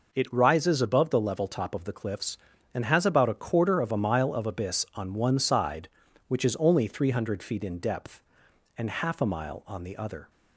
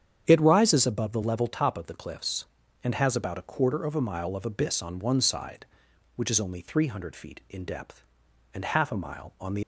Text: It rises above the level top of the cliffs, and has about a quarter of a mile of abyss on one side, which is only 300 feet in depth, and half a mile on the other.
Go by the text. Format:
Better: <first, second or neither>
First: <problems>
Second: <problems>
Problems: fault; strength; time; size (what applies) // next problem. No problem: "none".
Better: first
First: none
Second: starts louder than the rest; strong; until 1.2 s; 8.5 dB // stops before "other"; at 9.6 s